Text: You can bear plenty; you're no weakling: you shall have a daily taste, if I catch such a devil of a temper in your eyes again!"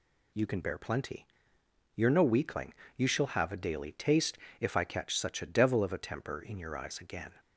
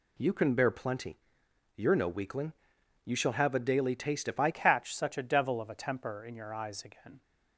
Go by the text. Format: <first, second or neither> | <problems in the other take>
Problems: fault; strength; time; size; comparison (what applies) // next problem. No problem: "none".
first | changes voice at "catch"; from 4.5 s on; 2.7 s long